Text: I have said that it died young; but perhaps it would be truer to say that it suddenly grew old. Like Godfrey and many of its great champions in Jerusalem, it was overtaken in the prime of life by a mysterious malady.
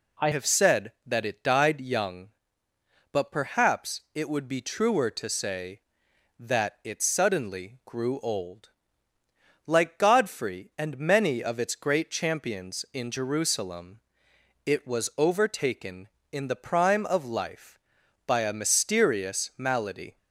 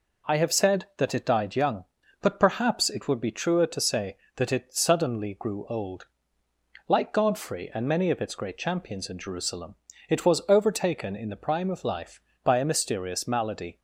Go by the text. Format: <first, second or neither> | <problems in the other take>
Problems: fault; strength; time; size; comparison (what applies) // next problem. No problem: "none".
second | changes voice at "have"; from 0.3 s on; 19.8 s long